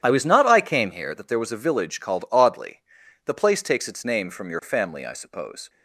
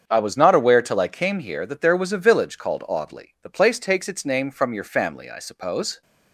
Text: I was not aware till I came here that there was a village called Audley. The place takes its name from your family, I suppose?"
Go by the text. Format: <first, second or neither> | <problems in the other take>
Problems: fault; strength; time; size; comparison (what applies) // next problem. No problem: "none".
second | starts louder than the rest; strong; until 1.0 s; 10 dB; strong in the second // skips "aware till"; at 0.4 s